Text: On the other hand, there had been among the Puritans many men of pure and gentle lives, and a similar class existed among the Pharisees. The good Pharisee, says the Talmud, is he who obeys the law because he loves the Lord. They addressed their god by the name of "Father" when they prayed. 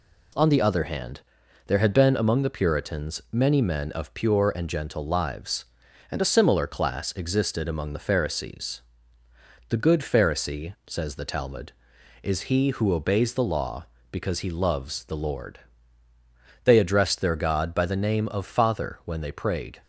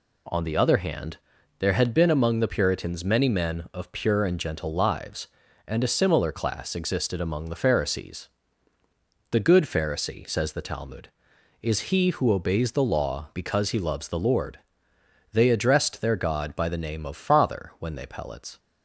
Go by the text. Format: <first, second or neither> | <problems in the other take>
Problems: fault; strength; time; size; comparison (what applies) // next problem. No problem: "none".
first | says "pellets" for "prayed"; at 18.0 s